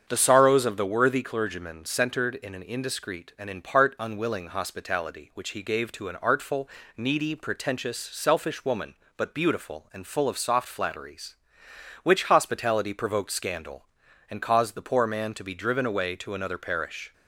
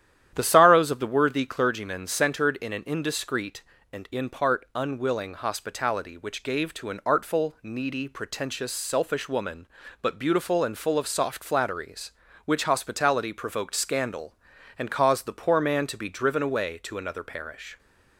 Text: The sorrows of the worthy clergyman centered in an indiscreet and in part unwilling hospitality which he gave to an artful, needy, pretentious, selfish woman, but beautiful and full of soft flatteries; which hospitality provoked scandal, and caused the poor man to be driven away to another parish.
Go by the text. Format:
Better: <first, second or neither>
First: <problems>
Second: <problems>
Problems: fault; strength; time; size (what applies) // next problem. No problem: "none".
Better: first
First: starts louder than the rest; strong; until 1.0 s; 7.5 dB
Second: starts louder than the rest; strong; until 1.3 s; 11 dB // skips "he"; at 6.4 s